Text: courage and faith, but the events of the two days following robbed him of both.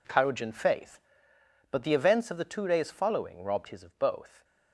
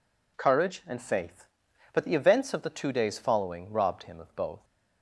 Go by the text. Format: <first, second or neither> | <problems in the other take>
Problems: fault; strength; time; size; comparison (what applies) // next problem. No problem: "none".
second | says "his" for "him"; at 3.6 s